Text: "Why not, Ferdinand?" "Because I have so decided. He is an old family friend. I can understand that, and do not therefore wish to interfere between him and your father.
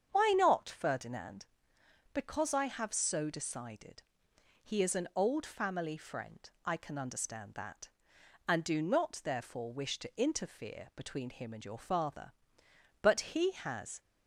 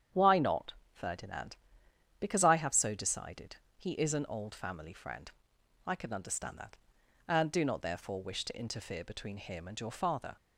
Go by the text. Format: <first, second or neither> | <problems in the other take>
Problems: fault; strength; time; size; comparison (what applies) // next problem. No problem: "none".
second | starts louder than the rest; strong; until 1.1 s; 7.5 dB; strong in the second // goes on to say "But he has"; noticeable; from 13.0 s on; 0.98 s long